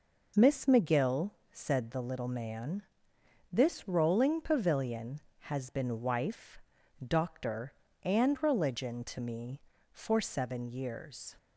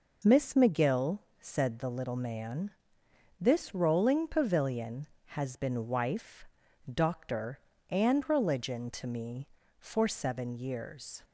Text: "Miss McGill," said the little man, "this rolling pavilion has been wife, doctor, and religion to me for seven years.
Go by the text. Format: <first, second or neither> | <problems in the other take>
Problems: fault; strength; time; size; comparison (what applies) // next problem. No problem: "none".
neither | none